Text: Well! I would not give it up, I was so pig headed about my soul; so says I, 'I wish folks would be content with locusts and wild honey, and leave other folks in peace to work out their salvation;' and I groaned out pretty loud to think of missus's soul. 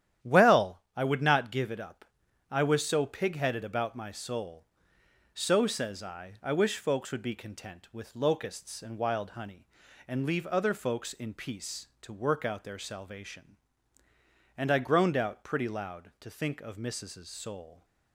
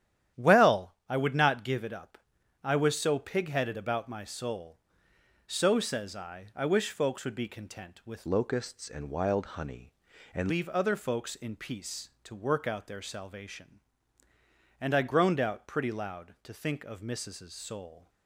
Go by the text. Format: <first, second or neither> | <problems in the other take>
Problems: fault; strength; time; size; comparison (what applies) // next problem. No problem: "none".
first | starts louder than the rest; strong; until 1.4 s; 11 dB; strong in the first // changes voice from "locusts" to "and"; from 8.2 to 10.4 s; 2.2 s long